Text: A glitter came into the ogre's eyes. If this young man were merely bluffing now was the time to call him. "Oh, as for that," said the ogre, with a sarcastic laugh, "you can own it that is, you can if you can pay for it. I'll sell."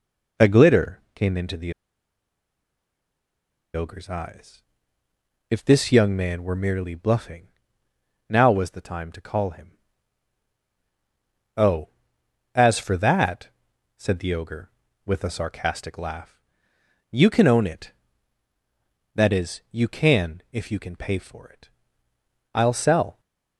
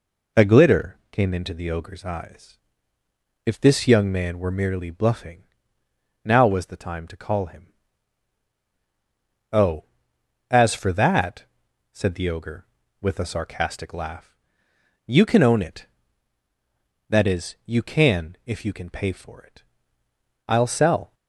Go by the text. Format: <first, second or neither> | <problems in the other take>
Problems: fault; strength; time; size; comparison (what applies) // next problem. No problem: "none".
second | pauses between "the" and "ogre's"; strong; at 1.7 s; 2.0 s long // pauses between "bluffing" and "now"; noticeable; at 7.4 s; 0.78 s long; noticeable in the second